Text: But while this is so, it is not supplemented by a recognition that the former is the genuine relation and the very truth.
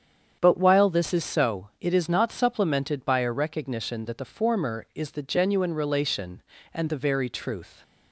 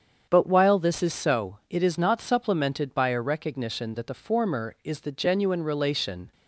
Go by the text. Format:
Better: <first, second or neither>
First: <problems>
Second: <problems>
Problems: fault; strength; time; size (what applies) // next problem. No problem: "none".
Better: first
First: starts louder than the rest; strong; until 1.4 s; 8 dB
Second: starts louder than the rest; strong; until 1.3 s; 7.5 dB // stops before "and the very truth"; at 6.3 s